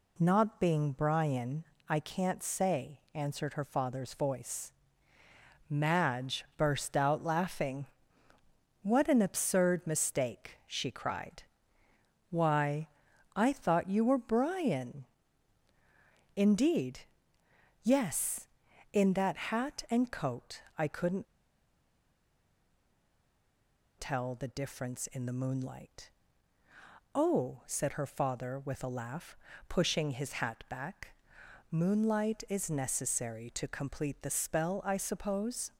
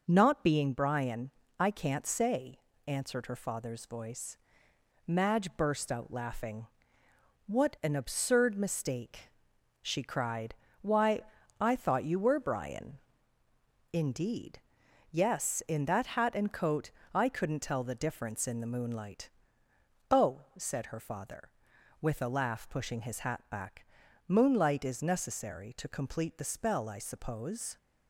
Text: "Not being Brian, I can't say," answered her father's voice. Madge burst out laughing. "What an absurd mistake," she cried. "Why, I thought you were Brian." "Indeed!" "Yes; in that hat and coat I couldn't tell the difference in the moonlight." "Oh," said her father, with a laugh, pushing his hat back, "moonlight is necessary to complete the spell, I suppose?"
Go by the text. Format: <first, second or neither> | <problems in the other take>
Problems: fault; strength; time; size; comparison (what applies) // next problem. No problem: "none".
second | pauses between "coat" and "I"; slight; at 20.6 s; 0.16 s long; slight in the second // pauses between "couldn't" and "tell"; strong; at 21.2 s; 2.7 s long